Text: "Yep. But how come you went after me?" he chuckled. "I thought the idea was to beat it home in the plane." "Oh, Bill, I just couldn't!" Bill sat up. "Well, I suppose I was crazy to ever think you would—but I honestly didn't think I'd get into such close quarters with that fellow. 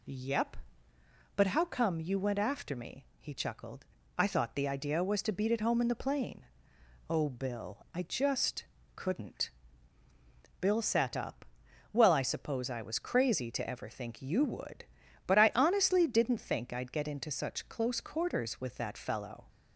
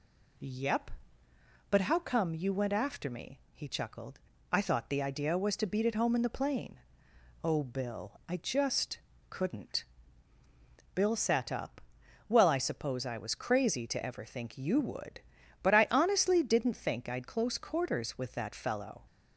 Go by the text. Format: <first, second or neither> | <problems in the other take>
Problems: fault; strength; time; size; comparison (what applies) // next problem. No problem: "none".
first | pauses between "just" and "couldn't"; slight; at 8.9 s; 0.32 s long; slight in the first // skips "get into such"; at 17.2 s